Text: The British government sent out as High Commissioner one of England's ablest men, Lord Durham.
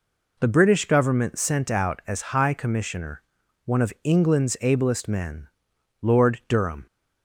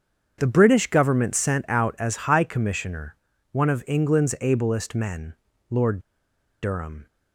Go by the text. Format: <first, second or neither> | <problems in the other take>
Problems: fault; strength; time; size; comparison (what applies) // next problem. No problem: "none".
first | starts louder than the rest; strong; until 1.4 s; 7.5 dB // pauses between "Commissioner" and "one"; slight; at 3.1 s; 0.36 s long; also in the first // pauses between "Lord" and "Durham"; noticeable; at 5.9 s; 0.63 s long